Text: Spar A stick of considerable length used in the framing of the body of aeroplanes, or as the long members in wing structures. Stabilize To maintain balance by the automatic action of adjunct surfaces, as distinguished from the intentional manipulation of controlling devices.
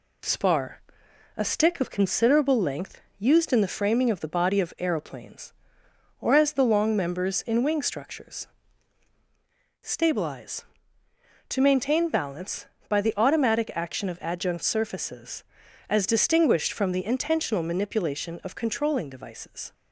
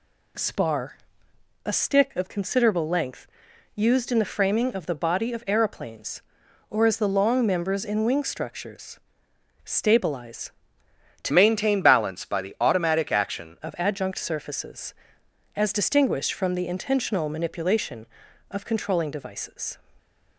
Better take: first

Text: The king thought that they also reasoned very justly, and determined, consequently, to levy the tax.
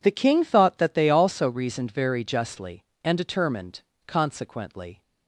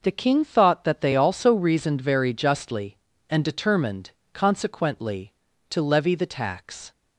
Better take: second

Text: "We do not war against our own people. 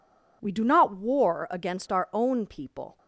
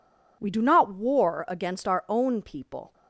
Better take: neither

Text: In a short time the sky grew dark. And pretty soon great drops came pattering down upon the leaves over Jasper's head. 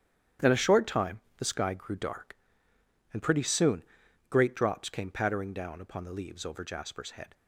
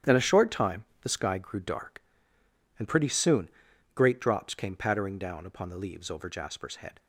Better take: neither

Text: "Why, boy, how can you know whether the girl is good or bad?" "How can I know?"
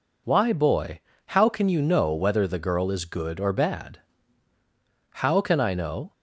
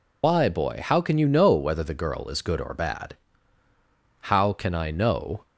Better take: first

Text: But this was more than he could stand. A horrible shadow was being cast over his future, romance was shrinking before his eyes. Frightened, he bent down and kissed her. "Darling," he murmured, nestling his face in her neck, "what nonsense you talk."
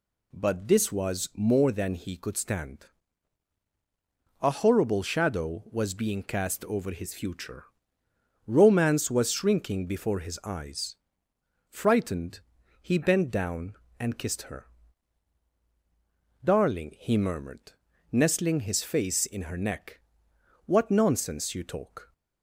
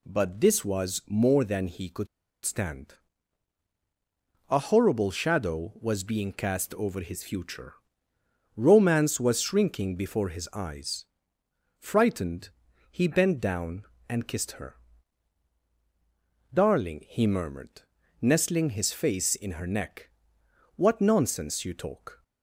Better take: first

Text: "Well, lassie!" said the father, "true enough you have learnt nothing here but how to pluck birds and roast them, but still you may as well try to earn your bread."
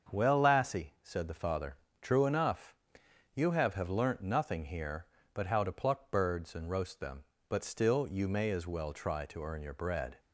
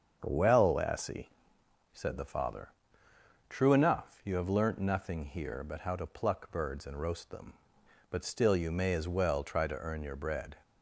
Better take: second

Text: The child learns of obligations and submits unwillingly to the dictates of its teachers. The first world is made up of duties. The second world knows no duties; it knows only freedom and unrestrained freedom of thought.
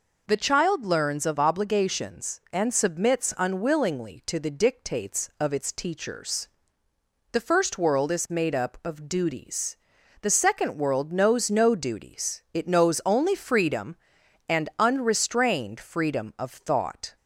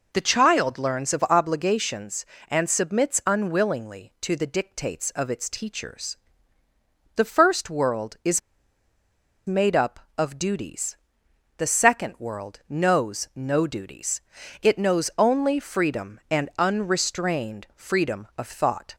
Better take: first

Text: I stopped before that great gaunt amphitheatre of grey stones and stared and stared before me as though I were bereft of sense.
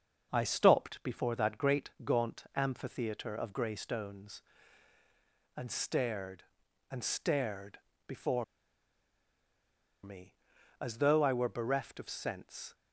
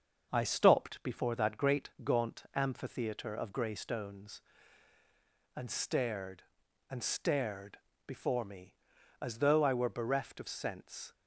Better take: second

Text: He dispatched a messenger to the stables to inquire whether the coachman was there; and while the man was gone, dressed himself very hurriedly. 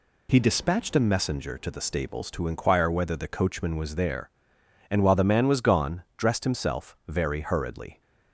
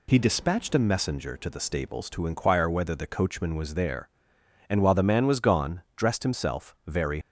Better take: first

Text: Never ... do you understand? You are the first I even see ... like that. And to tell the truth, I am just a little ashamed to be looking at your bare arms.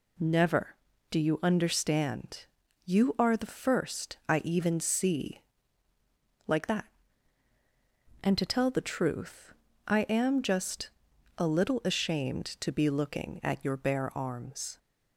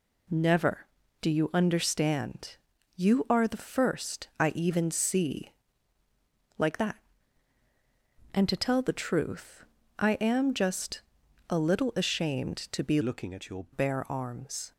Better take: first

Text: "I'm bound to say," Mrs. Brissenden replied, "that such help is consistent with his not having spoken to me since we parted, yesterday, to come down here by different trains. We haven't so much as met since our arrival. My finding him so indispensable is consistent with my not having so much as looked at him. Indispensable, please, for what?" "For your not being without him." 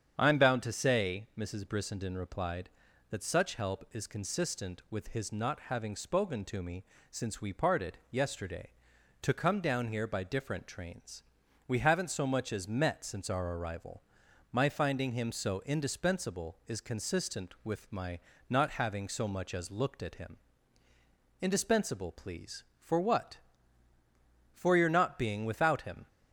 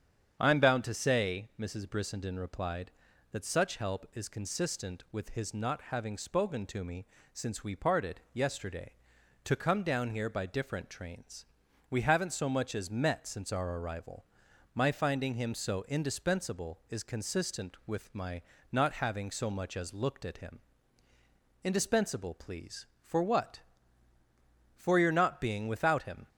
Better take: neither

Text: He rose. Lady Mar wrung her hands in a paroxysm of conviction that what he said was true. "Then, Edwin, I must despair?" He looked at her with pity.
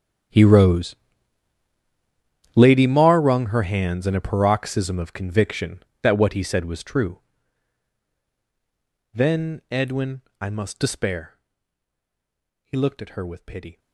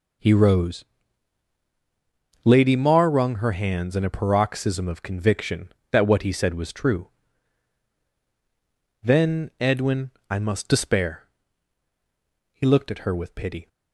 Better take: second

